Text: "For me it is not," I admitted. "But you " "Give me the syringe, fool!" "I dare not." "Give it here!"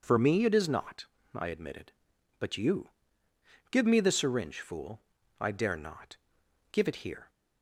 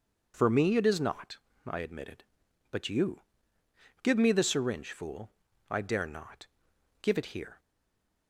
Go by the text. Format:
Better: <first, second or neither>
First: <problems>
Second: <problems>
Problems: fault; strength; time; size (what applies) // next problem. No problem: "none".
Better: first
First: none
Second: stays silent after the last word; slight; from 7.5 s on; 0.7 s long